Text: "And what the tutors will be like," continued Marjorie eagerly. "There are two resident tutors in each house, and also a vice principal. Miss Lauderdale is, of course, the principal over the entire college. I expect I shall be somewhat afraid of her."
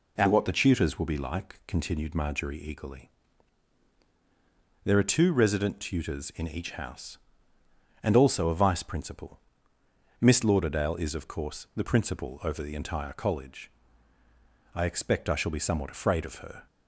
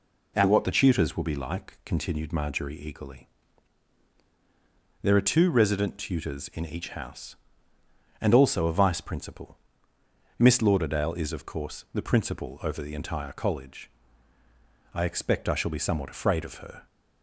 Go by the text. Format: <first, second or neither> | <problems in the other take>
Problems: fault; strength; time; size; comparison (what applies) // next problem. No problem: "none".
neither | none